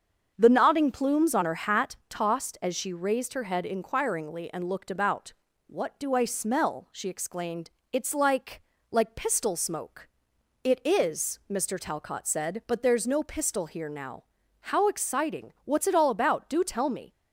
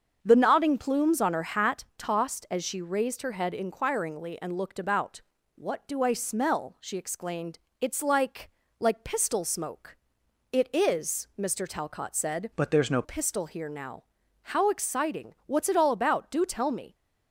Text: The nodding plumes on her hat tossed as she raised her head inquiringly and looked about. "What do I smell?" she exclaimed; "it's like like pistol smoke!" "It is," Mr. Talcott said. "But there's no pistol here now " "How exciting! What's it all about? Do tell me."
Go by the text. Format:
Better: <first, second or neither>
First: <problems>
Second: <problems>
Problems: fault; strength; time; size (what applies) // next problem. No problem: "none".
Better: first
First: starts louder than the rest; until 1.3 s; 7 dB // pauses between "like" and "like"; slight; at 8.6 s; 0.30 s long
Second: starts louder than the rest; until 1.2 s; 7 dB // pauses between "like" and "like"; slight; at 8.5 s; 0.30 s long // changes voice from "But" to "no"; from 12.5 to 13.0 s; 0.5 s long